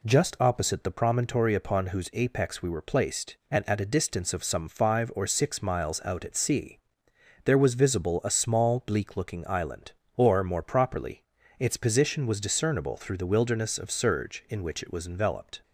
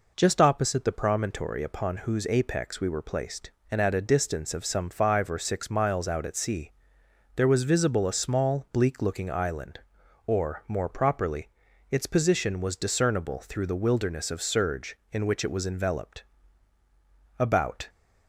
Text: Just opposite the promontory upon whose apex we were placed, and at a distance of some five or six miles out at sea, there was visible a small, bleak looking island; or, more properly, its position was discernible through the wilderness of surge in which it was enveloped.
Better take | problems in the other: first | goes on to say "About"; slight; from 17.3 s on; 0.48 s long

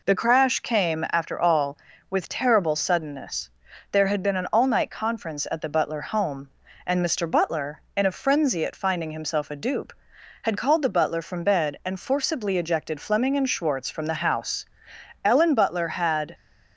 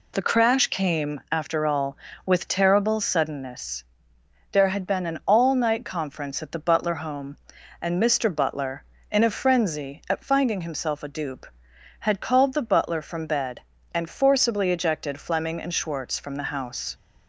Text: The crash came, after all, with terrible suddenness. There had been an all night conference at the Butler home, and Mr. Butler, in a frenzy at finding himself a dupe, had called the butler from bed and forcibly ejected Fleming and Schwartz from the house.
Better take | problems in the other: second | goes on to say "Ellen Butler had"; noticeable; from 15.2 s on; 1.1 s long

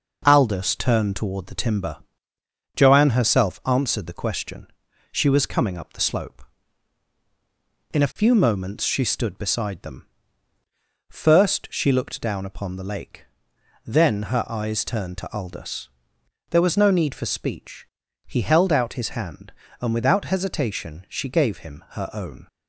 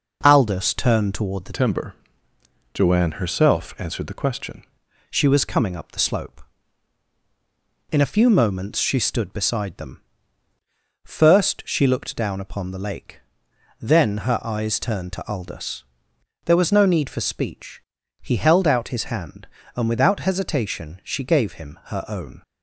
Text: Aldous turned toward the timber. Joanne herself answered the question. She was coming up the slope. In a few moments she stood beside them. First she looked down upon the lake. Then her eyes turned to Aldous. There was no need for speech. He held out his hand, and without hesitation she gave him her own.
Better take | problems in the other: first | changes voice from "timber" to "question"; from 1.5 to 4.6 s; 3.1 s long

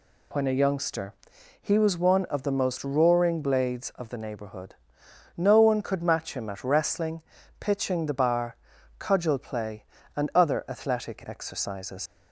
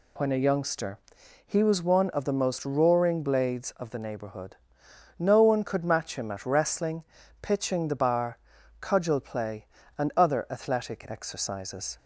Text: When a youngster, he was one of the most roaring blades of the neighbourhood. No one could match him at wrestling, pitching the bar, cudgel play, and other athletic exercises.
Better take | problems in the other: second | leaves "exercises" unfinished; at 12.0 s; 90 ms

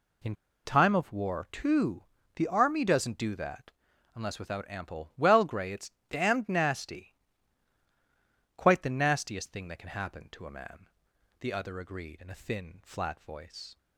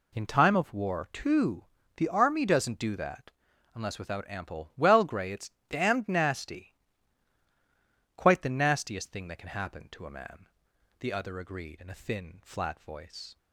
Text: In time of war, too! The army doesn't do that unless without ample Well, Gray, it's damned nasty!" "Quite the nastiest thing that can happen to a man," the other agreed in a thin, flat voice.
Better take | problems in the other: second | pauses between "In" and "time"; slight; at 0.3 s; 0.29 s long // pauses between "that" and "unless"; at 3.7 s; 0.42 s long; also in the second // pauses between "it's" and "damned"; slight; at 5.9 s; 0.18 s long; slight in the second

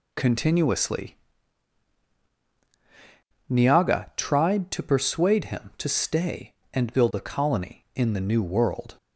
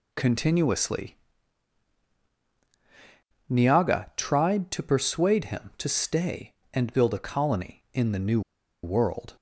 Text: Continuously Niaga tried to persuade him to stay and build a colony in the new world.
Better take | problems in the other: first | pauses between "Continuously" and "Niaga"; strong; at 1.1 s; 2.3 s long; strong in the first // pauses between "new" and "world"; at 8.4 s; 0.43 s long

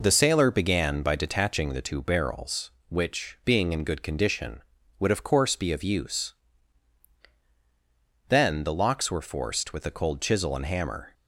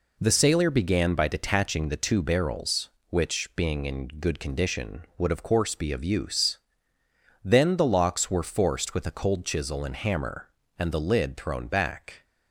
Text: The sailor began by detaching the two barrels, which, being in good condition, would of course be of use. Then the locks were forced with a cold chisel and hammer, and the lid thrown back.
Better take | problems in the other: second | stops before "and the lid thrown back"; at 11.1 s

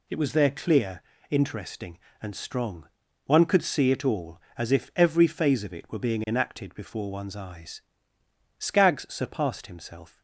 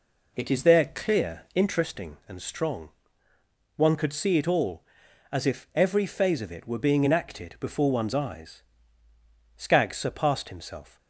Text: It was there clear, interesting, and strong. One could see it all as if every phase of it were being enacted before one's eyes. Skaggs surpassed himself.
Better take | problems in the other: first | says "is" for "was"; at 0.5 s

